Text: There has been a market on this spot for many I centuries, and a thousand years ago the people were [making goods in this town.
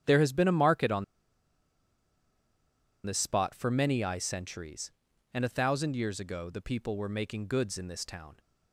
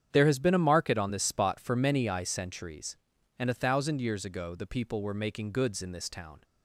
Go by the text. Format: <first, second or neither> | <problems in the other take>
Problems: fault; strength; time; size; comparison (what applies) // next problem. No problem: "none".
second | starts louder than the rest; strong; until 3.0 s; 9 dB; strong in the second // pauses between "on" and "this"; strong; at 1.0 s; 2.0 s long